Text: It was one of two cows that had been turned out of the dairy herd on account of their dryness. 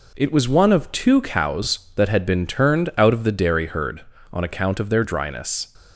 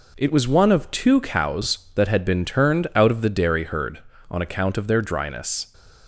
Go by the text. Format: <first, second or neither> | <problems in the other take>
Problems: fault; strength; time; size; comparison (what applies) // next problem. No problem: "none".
neither | none